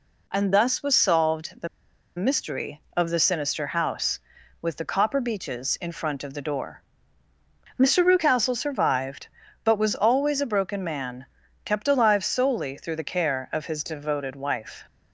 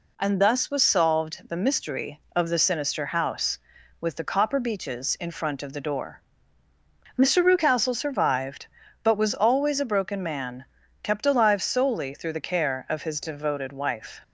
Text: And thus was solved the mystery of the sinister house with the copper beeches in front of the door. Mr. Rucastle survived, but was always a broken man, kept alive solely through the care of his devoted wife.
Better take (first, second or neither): second